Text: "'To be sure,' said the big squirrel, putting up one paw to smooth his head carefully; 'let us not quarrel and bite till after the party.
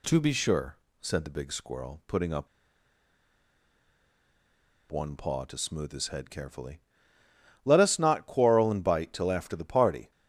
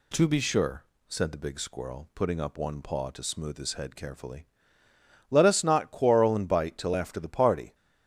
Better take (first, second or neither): second